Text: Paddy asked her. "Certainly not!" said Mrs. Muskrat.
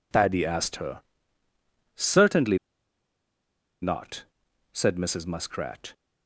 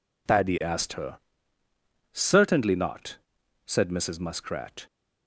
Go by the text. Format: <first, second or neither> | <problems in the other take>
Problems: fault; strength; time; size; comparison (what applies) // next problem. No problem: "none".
second | pauses between "Certainly" and "not"; at 2.5 s; 1.2 s long